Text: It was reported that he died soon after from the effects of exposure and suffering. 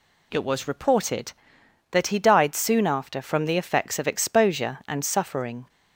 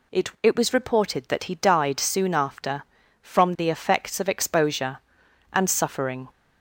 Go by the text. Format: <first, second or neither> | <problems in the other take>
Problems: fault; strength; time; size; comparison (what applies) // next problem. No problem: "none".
first | says "It" twice; at 0.4 s